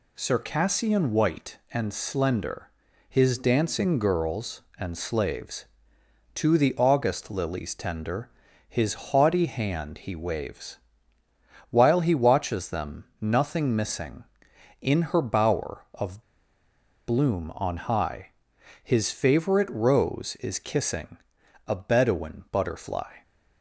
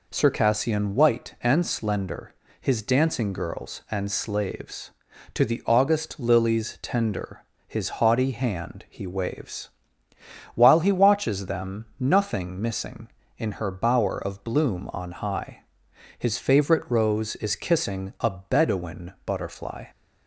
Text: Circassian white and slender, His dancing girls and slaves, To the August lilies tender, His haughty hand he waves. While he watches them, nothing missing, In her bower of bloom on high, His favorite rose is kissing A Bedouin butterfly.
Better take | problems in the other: second | pauses between "of" and "bloom"; noticeable; at 16.2 s; 0.83 s long // pauses between "kissing" and "A"; noticeable; at 21.1 s; 0.50 s long

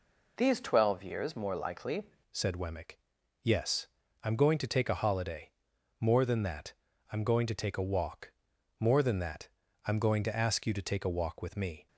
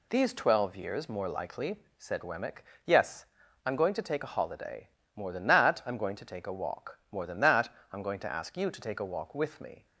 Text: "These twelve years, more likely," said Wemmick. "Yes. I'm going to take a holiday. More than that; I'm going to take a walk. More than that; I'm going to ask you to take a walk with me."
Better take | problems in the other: second | changes voice at "said"; from 2.3 s on; 9.5 s long

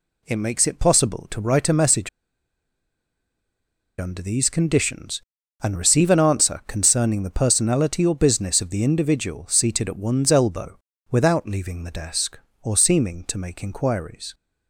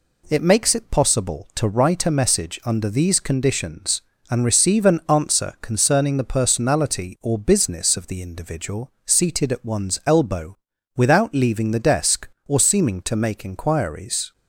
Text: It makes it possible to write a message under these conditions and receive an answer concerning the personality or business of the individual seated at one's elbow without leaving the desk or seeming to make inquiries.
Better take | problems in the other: second | pauses between "message" and "under"; strong; at 2.0 s; 1.9 s long // pauses between "elbow" and "without"; slight; at 10.7 s; 0.32 s long; also in the second

